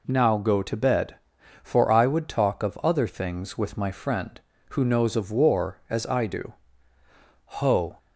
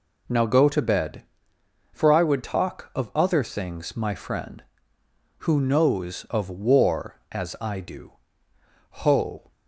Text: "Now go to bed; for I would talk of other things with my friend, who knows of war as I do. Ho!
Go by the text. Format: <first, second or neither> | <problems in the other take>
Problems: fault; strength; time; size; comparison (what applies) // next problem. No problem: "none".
first | skips "with"; at 3.9 s